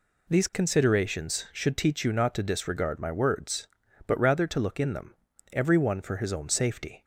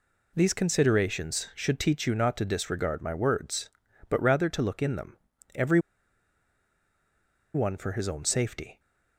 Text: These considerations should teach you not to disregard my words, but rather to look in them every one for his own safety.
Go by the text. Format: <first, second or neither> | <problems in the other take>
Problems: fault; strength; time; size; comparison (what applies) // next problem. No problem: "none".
first | pauses between "them" and "every"; at 5.1 s; 0.38 s long; also in the first // pauses between "every" and "one"; strong; at 5.7 s; 1.7 s long